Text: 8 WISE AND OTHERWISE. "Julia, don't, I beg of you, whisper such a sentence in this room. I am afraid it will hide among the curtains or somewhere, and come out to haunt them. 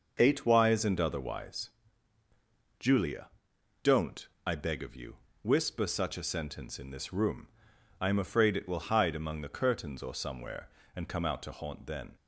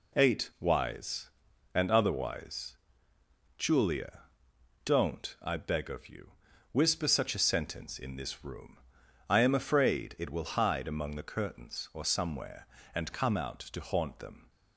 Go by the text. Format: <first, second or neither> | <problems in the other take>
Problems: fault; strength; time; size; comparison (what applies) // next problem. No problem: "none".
second | says "then" for "them"; at 11.8 s